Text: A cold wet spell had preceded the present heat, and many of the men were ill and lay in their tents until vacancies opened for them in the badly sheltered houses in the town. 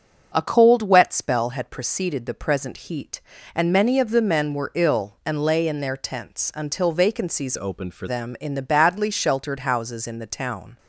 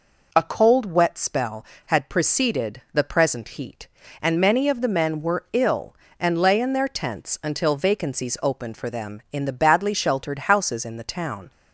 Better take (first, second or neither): second